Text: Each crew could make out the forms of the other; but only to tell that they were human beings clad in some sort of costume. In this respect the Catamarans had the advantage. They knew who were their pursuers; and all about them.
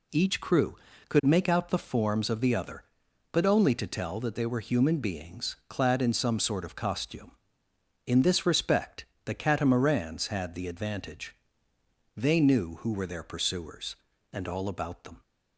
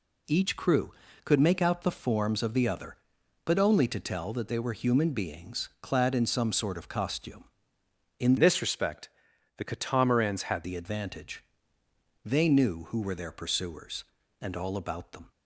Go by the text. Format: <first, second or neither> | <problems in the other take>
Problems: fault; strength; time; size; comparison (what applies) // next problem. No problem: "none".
first | changes voice from "this" to "had"; from 8.3 to 10.6 s; 2.3 s long // pauses between "respect" and "the"; noticeable; at 9.0 s; 0.48 s long; slight in the first